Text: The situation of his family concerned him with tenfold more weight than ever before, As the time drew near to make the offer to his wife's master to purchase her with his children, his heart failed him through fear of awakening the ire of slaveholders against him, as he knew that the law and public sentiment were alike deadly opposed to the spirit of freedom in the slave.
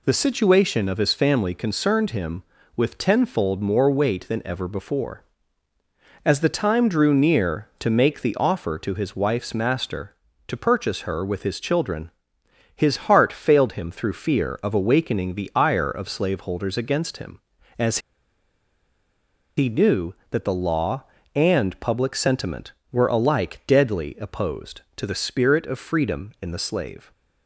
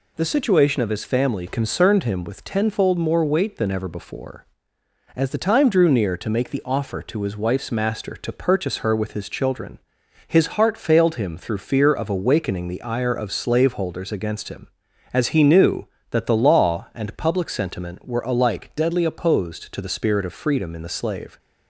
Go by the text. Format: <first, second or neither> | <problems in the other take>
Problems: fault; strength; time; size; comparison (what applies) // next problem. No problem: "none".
second | pauses between "as" and "he"; strong; at 17.9 s; 1.5 s long